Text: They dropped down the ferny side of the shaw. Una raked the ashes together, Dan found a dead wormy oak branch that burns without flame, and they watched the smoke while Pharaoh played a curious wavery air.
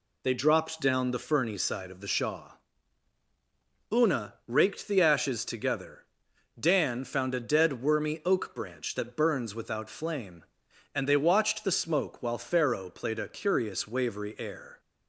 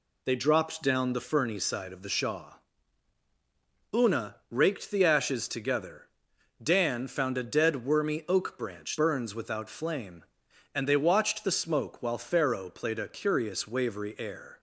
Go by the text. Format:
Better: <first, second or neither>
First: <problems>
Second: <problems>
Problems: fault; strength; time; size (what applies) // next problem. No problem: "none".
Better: first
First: none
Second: skips "that"; at 8.9 s